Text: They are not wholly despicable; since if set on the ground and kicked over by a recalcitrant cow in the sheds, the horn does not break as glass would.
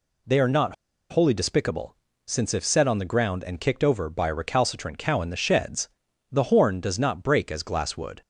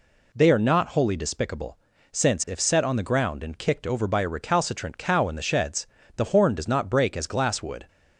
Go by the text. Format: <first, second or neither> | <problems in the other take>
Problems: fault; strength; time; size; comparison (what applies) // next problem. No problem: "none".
second | pauses between "not" and "wholly"; at 0.7 s; 0.36 s long